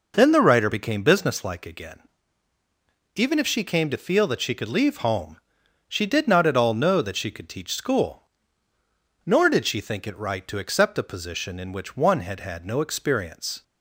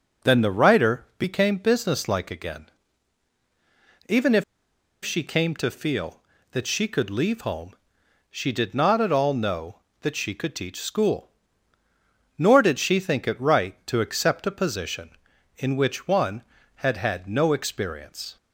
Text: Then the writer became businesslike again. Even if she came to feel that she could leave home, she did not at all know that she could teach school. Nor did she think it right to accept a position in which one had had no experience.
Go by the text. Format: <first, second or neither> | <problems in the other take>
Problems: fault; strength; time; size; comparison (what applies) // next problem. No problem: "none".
first | pauses between "if" and "she"; noticeable; at 4.4 s; 0.60 s long